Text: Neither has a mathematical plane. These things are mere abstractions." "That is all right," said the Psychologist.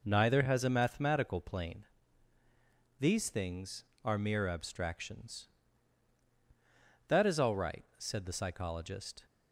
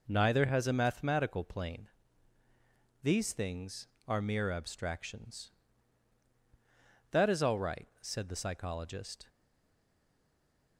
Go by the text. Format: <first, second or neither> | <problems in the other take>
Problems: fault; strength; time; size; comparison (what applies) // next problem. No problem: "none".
first | stays silent after the last word; noticeable; from 9.2 s on; 1.5 s long